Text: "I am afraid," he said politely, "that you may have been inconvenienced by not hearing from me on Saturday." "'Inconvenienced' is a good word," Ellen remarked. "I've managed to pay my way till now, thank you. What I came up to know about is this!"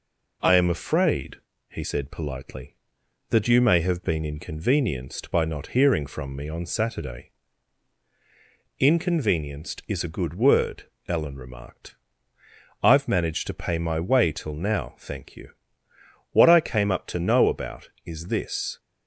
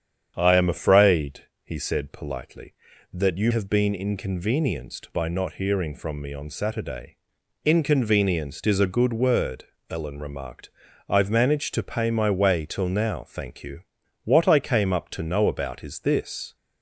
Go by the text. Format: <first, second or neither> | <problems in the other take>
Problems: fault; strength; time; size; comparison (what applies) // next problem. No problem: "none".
first | starts louder than the rest; strong; until 1.3 s; 8 dB // skips "may"; at 3.5 s